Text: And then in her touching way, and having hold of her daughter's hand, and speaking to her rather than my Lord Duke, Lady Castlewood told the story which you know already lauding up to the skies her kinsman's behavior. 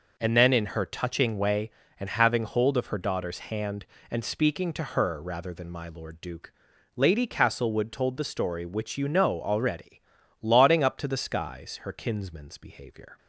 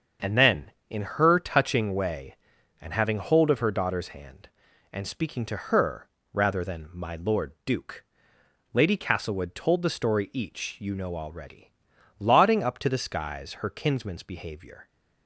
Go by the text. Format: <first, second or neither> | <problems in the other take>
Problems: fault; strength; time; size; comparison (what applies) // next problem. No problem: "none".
first | starts louder than the rest; until 1.3 s; 7 dB // pauses between "her" and "rather"; slight; at 6.0 s; 0.26 s long // says "each" for "which"; at 10.3 s // pauses between "already" and "lauding"; noticeable; at 11.6 s; 0.56 s long; also in the first